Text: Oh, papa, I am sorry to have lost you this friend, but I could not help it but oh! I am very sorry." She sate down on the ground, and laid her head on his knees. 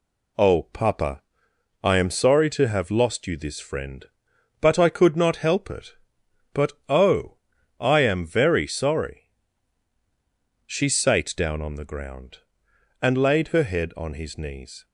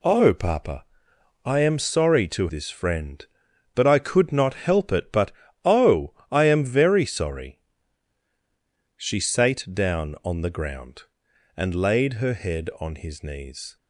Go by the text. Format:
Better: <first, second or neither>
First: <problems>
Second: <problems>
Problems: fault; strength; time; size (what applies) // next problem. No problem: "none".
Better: first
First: pauses between "but" and "oh"; slight; at 6.7 s; 0.16 s long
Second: skips "have lost you"; at 2.4 s // pauses between "but" and "oh"; slight; at 5.3 s; 0.32 s long